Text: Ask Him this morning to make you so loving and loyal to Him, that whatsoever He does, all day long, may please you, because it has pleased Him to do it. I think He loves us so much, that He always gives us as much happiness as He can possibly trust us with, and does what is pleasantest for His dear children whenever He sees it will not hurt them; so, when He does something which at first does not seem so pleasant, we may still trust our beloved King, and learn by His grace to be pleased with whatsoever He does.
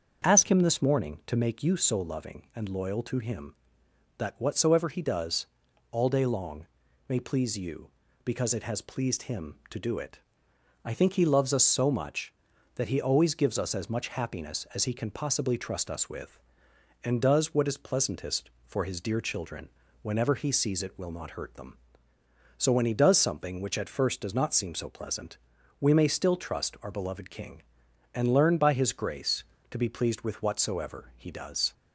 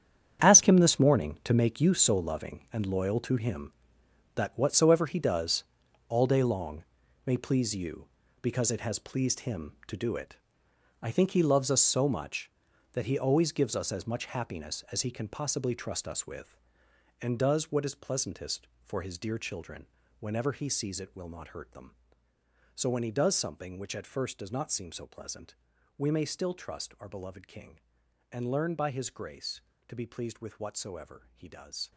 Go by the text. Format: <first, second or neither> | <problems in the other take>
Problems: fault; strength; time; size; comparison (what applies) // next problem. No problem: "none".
first | gets quieter; strong; throughout; 13.5 dB // starts louder than the rest; strong; until 1.5 s; 8.5 dB; also in the first // pauses between "children" and "whenever"; slight; at 19.8 s; 0.36 s long; slight in the first